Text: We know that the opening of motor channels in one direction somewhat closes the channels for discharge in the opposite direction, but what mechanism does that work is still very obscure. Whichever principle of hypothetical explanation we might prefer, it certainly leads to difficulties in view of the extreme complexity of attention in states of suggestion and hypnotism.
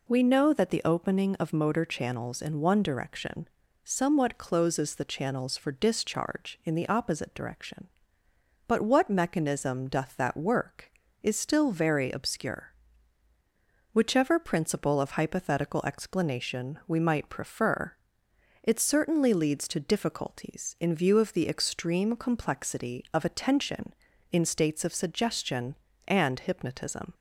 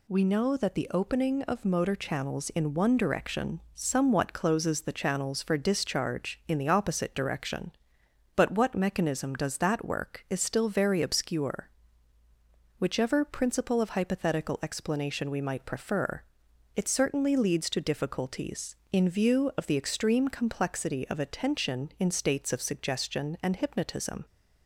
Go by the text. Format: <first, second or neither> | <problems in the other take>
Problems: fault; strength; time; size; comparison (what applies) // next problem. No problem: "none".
second | pauses between "direction" and "somewhat"; slight; at 3.4 s; 0.36 s long // says "doth" for "does"; at 9.8 s